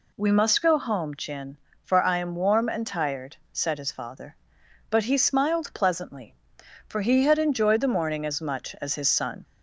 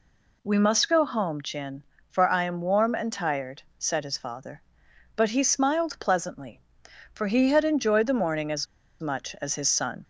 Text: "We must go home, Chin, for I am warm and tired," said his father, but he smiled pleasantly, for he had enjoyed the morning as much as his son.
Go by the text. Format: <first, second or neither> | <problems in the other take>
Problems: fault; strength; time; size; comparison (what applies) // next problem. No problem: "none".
first | pauses between "as" and "much"; slight; at 8.6 s; 0.34 s long